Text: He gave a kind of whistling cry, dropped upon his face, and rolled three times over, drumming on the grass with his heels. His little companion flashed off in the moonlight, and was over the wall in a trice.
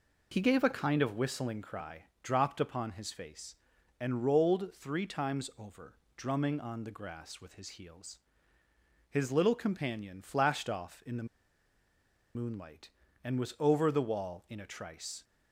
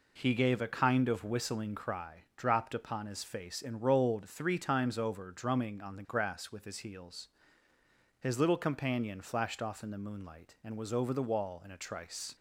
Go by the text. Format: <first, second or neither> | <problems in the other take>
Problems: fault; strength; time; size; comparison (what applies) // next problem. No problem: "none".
second | pauses between "the" and "moonlight"; at 11.2 s; 1.1 s long